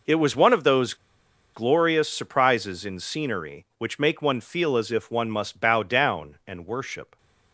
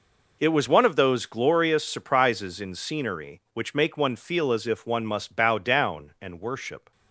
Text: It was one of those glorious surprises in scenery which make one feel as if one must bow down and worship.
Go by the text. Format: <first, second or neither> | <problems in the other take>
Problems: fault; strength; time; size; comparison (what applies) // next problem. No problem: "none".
second | pauses between "those" and "glorious"; noticeable; at 0.9 s; 0.59 s long